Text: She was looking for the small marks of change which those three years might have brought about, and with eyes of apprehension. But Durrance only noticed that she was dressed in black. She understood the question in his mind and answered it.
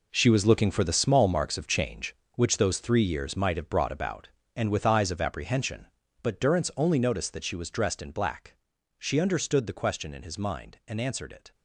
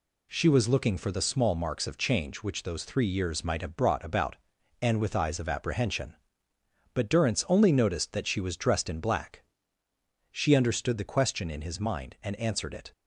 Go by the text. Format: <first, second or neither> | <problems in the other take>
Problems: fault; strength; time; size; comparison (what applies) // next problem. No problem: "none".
second | gets quieter; strong; throughout; 10.5 dB